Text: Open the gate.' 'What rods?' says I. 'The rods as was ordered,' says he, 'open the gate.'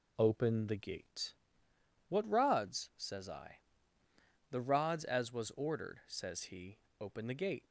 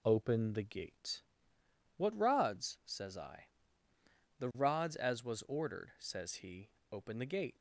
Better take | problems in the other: neither | none

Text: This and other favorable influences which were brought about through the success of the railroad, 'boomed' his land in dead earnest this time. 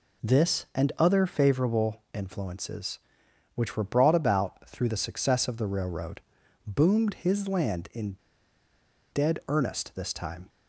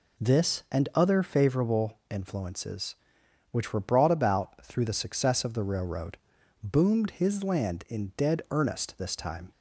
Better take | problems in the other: second | pauses between "in" and "dead"; noticeable; at 8.1 s; 0.96 s long

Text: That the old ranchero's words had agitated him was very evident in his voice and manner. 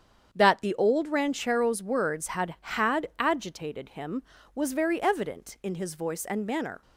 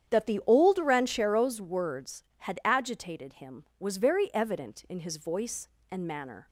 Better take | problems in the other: second | starts louder than the rest; strong; until 1.3 s; 8 dB; strong in the second // says "had" twice; at 2.6 s

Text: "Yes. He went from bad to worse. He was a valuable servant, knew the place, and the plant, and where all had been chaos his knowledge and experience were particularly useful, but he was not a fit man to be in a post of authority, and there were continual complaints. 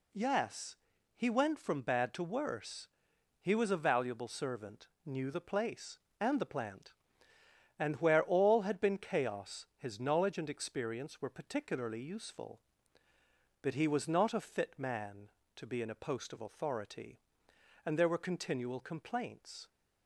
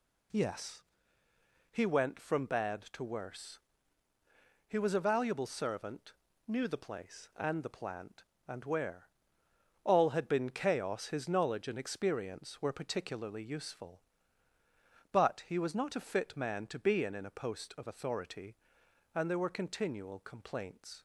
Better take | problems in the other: first | pauses between "where" and "all"; noticeable; at 9.0 s; 0.74 s long // says "in" twice; at 17.1 s

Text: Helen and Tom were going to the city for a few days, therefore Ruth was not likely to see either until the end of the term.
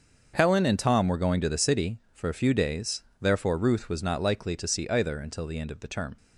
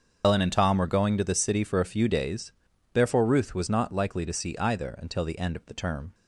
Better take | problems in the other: first | loses the start of "Helen"; at 0.2 s; 95 ms // starts louder than the rest; until 1.2 s; 7 dB; also in the first

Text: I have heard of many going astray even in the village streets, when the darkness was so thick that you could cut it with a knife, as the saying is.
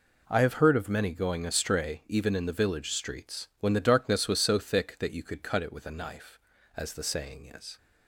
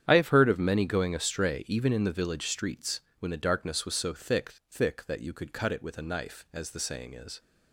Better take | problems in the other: first | starts louder than the rest; strong; until 1.0 s; 9 dB // says "thick" twice; at 4.6 s

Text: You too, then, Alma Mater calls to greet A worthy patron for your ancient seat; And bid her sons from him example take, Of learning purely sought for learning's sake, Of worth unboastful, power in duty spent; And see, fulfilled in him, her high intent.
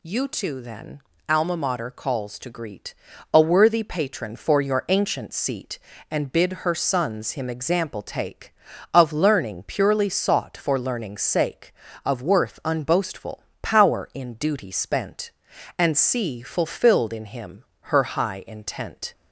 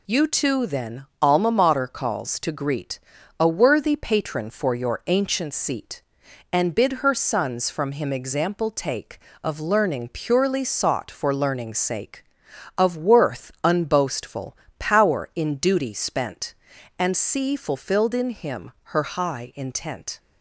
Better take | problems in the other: second | pauses between "greet" and "A"; at 2.9 s; 0.40 s long; also in the second // skips "from"; at 7.3 s

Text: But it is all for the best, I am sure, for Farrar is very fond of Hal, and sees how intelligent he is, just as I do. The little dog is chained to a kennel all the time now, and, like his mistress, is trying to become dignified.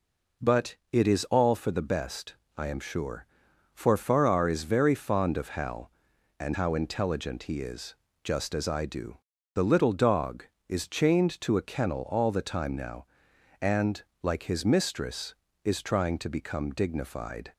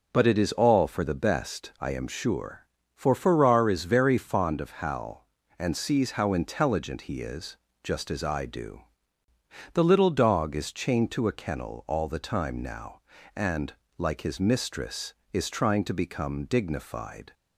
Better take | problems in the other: second | pauses between "But" and "it"; slight; at 0.7 s; 0.16 s long // skips "sees"; at 6.5 s

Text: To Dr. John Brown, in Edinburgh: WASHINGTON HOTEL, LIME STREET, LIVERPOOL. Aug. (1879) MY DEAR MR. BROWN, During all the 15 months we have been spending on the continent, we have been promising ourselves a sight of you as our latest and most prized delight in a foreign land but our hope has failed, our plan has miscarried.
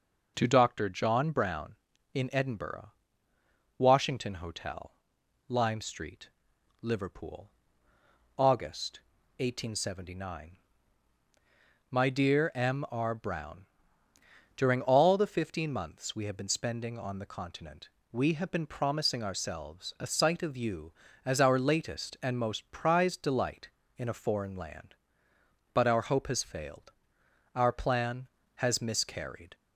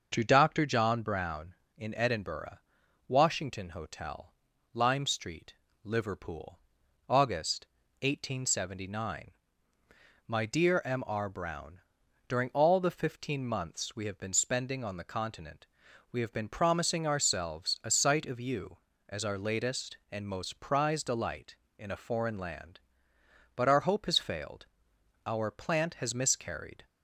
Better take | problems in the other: first | starts louder than the rest; until 1.1 s; 6.5 dB // says "plant" for "plan"; at 25.4 s

